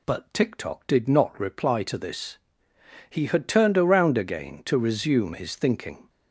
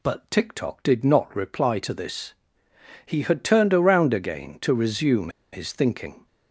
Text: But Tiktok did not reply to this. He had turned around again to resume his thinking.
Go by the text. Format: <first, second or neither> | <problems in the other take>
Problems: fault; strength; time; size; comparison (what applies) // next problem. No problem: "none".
first | pauses between "resume" and "his"; slight; at 5.2 s; 0.23 s long